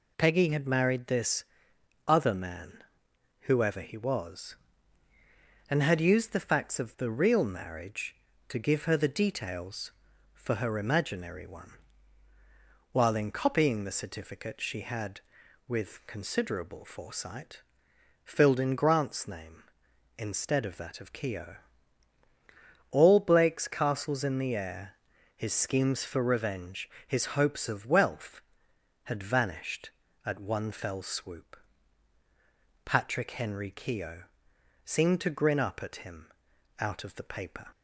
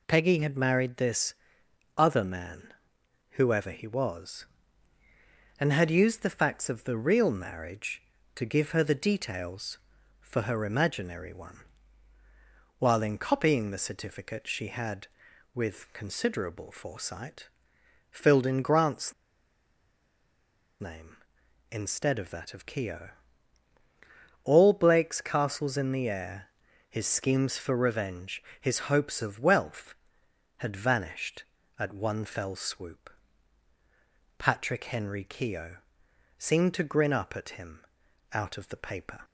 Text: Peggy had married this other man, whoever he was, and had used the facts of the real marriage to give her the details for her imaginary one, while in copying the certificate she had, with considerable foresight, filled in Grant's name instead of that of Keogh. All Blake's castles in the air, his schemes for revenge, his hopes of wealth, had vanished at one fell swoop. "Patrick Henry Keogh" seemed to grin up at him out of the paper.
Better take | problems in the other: first | pauses between "this" and "other"; noticeable; at 1.3 s; 0.62 s long; noticeable in the first // pauses between "Grant's" and "name"; strong; at 19.1 s; 1.6 s long // pauses between "Keogh" and "seemed"; noticeable; at 35.7 s; 0.60 s long; noticeable in the first // pauses between "him" and "out"; noticeable; at 37.8 s; 0.48 s long; noticeable in the first

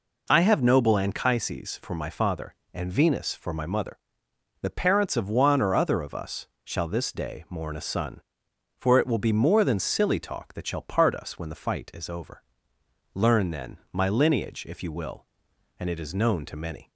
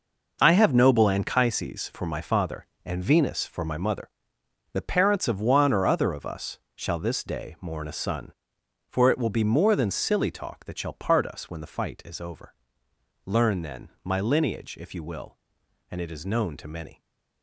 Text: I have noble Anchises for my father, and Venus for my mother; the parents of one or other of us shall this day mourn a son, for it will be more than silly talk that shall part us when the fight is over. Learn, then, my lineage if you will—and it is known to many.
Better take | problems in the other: first | gets quieter; strong; throughout; 10 dB // pauses between "us" and "shall"; slight; at 6.5 s; 0.16 s long; slight in the first

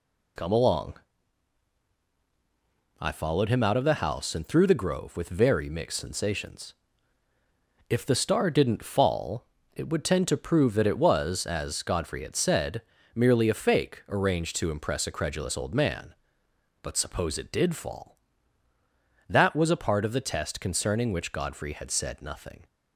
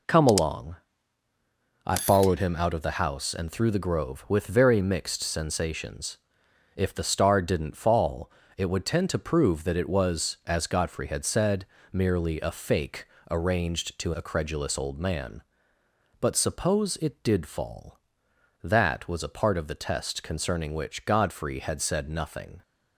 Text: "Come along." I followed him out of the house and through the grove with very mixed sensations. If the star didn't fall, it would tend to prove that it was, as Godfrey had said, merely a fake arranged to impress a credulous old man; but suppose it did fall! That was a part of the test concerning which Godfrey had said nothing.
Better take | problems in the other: first | pauses between "fake" and "arranged"; slight; at 13.0 s; 0.26 s long // skips "impress"; at 14.1 s

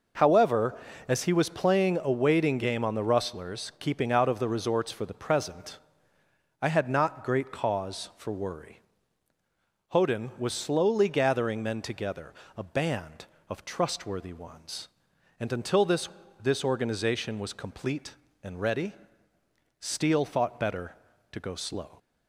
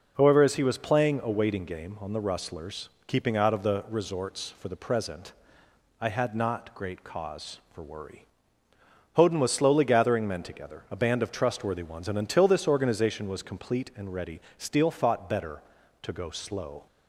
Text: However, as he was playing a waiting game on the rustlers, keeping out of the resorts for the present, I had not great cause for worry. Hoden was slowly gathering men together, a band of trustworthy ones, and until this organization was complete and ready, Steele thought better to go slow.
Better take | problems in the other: second | says "this" twice; at 16.4 s

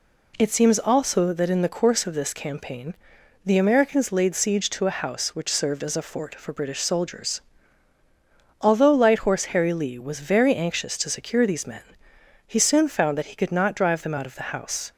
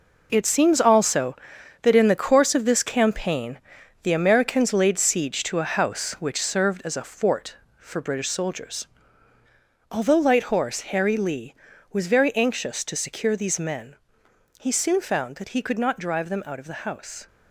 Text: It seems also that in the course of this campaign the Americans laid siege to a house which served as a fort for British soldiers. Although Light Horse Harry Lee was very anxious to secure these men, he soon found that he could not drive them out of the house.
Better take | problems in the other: first | gets quieter; strong; throughout; 9.5 dB // pauses between "campaign" and "the"; at 3.5 s; 0.44 s long; noticeable in the first

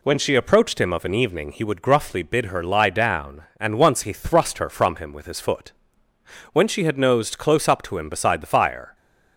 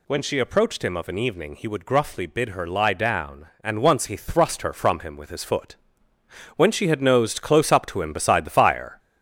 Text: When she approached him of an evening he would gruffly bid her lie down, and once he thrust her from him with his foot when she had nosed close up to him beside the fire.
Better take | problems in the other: first | gets louder; noticeable; throughout; 5 dB // pauses between "foot" and "when"; noticeable; at 5.7 s; 0.80 s long; noticeable in the first

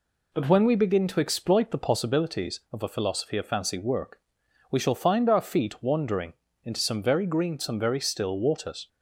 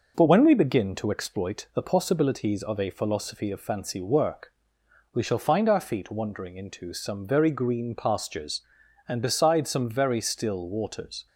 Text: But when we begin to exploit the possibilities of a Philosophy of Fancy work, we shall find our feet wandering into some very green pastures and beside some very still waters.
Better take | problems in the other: second | pauses between "wandering" and "into"; slight; at 6.3 s; 0.32 s long // skips "pastures and beside"; at 7.5 s

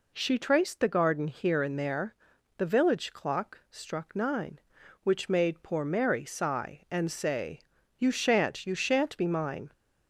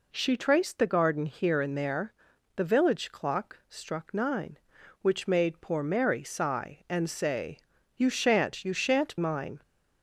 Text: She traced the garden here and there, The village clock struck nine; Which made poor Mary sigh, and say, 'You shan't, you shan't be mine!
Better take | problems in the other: first | skips "be"; at 9.1 s

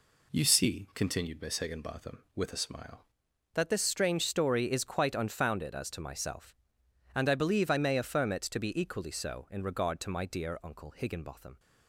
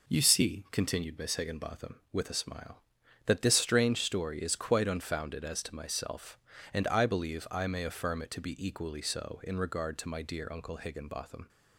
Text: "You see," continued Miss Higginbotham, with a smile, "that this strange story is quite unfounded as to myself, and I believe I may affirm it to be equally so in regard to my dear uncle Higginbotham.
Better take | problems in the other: second | changes voice at "that"; from 3.5 s on; 8.0 s long

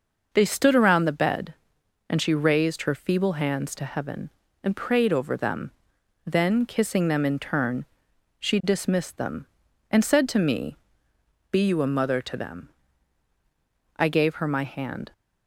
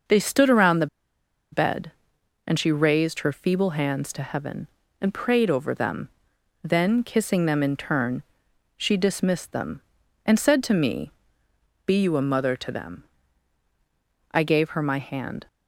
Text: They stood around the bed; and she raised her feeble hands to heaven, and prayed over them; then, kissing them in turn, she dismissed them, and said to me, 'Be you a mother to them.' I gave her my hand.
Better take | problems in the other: first | starts louder than the rest; noticeable; until 1.7 s; 6 dB // pauses between "the" and "bed"; noticeable; at 0.8 s; 0.66 s long

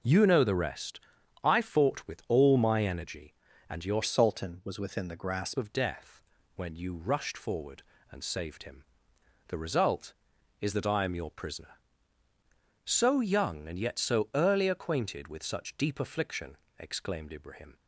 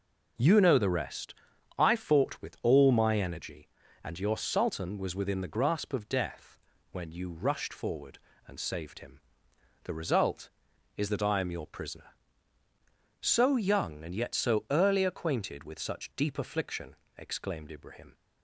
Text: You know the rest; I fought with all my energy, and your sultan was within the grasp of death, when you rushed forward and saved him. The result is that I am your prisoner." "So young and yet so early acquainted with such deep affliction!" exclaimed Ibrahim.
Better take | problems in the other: second | changes voice from "sultan" to "grasp"; from 4.0 to 5.5 s; 1.5 s long

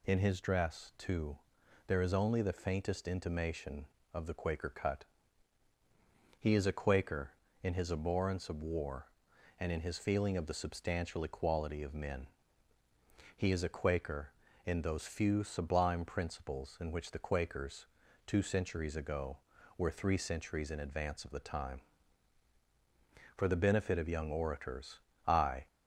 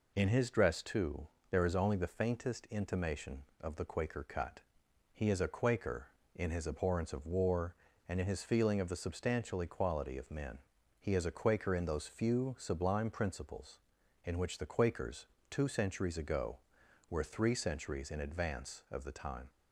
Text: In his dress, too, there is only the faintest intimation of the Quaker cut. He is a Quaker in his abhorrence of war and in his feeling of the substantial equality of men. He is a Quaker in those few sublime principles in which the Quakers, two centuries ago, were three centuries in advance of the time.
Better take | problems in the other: second | goes on to say "For the benefit of young orators I"; strong; from 23.3 s on; 2.3 s long

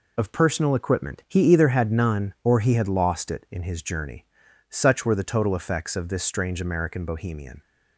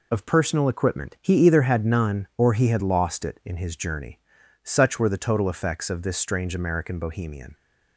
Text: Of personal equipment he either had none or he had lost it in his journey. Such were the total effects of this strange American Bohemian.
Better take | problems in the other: neither | none

